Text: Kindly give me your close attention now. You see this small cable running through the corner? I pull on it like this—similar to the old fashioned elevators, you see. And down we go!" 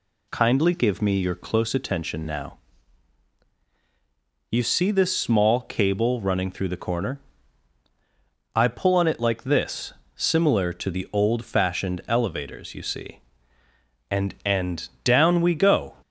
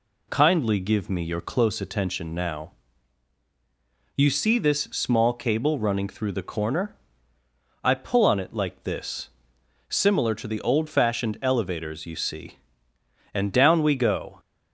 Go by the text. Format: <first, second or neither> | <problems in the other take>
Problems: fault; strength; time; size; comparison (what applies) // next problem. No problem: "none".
second | says "And" twice; at 14.4 s